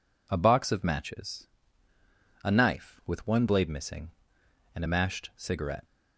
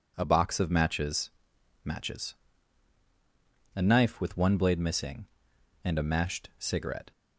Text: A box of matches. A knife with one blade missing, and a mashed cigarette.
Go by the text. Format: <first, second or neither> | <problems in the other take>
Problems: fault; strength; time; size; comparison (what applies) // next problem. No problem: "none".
first | says "matches" twice; at 1.8 s